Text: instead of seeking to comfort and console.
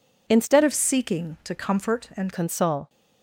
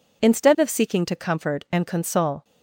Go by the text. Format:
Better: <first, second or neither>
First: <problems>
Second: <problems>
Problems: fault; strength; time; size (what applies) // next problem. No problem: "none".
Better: second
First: changes voice from "of" to "and"; from 0.6 to 2.3 s; 1.7 s long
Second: none